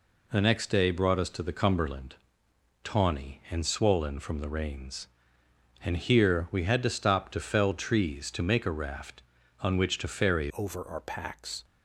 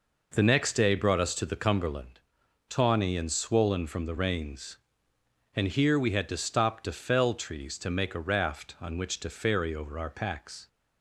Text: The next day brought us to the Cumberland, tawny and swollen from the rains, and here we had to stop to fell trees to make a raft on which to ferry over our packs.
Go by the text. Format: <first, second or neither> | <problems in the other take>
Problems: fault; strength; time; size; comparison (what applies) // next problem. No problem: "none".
second | changes voice at "over"; from 10.5 s on; 1.1 s long